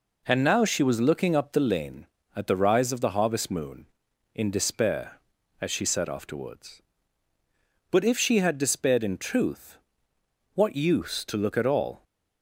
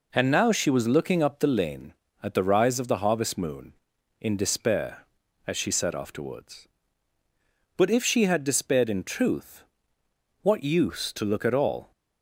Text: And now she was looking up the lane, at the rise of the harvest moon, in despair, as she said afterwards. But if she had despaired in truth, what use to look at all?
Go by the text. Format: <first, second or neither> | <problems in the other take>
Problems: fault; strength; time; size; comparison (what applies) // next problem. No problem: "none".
neither | none